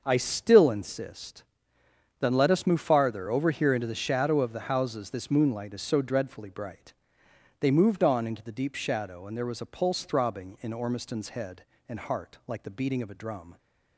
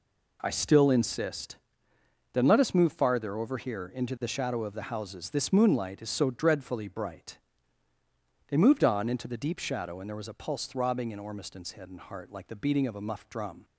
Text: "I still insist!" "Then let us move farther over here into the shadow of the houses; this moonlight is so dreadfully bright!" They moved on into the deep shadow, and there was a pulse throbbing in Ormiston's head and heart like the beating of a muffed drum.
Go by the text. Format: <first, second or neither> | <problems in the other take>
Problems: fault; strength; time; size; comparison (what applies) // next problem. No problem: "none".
second | starts louder than the rest; until 1.0 s; 6 dB // skips "muffed"; at 13.1 s